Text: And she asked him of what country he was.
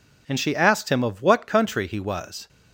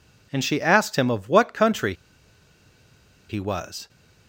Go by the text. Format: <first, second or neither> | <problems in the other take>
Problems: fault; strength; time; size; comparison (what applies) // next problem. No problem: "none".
first | pauses between "country" and "he"; strong; at 1.9 s; 1.3 s long